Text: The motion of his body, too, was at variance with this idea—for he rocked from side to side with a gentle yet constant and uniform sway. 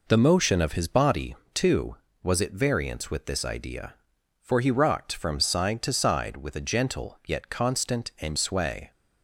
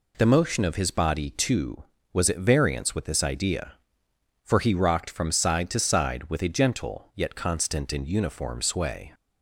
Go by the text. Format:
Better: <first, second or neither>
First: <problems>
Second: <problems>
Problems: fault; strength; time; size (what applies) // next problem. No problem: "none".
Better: second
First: skips "uniform"; at 8.3 s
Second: none